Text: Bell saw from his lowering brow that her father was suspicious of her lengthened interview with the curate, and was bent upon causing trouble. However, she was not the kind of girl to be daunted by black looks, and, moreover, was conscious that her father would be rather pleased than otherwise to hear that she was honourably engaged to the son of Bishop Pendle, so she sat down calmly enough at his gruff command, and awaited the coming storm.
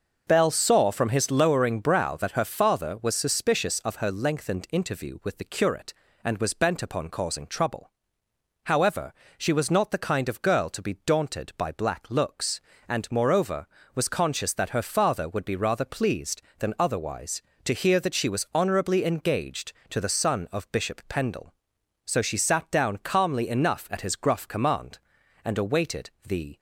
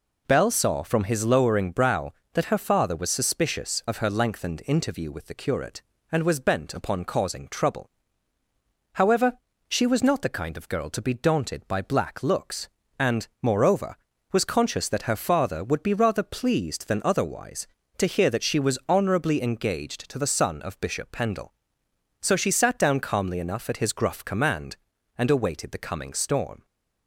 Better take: second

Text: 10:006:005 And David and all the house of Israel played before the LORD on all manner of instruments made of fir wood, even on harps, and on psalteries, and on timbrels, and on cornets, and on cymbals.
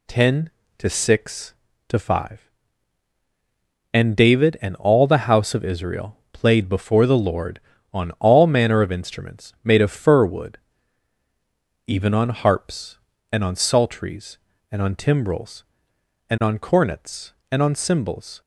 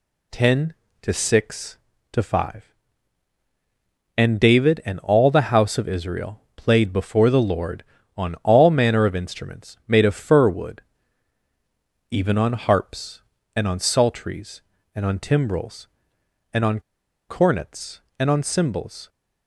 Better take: first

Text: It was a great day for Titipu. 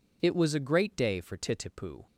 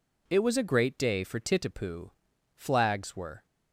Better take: first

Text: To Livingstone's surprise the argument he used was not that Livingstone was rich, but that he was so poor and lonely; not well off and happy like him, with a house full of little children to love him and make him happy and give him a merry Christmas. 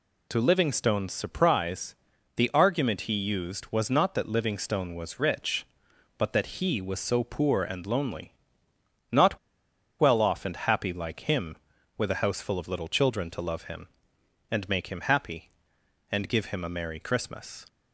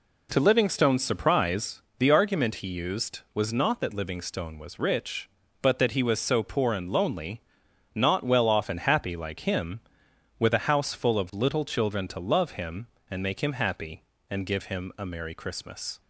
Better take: second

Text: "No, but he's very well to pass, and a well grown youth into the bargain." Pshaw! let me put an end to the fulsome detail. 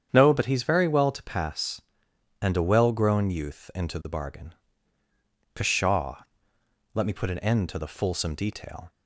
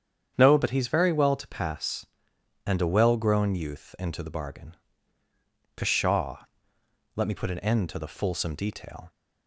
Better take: neither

